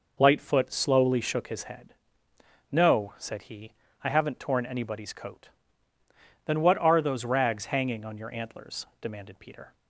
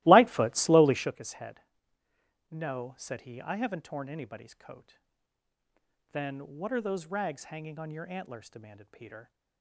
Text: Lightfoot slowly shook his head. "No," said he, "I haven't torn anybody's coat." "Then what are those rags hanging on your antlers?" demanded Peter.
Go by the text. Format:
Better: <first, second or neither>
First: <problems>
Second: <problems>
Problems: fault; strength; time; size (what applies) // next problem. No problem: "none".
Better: first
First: none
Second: starts louder than the rest; strong; until 1.1 s; 17.5 dB